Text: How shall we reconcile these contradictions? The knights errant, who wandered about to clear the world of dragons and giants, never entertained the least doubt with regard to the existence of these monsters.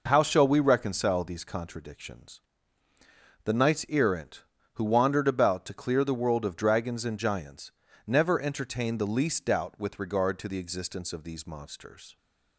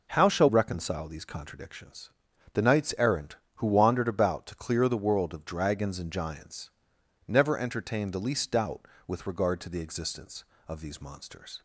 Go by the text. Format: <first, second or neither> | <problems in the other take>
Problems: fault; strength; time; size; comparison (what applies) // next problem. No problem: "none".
first | skips "we"; at 0.4 s